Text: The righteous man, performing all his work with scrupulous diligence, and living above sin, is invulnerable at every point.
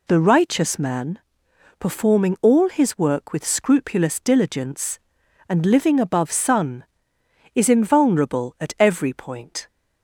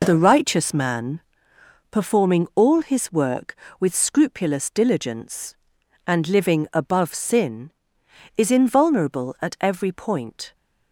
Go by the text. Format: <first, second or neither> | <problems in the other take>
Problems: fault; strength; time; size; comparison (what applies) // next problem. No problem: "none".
second | says "sun" for "sin"; at 6.3 s